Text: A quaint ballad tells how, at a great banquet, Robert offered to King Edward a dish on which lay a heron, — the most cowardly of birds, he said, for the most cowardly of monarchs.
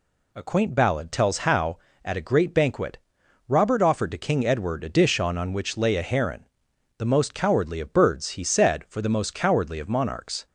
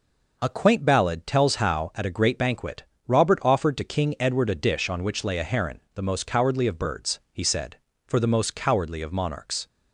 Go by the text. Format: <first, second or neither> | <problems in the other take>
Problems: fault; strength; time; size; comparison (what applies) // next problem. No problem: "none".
second | says "on" twice; at 5.3 s